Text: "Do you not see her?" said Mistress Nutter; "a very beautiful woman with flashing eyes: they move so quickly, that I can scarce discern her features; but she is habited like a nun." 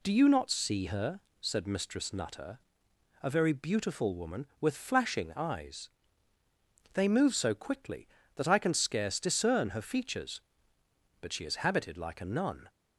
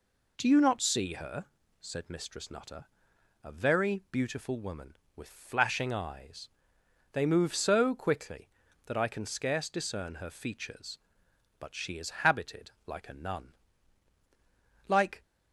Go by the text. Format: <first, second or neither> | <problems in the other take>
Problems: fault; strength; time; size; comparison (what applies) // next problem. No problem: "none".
first | goes on to say "Like"; slight; from 14.8 s on; 0.34 s long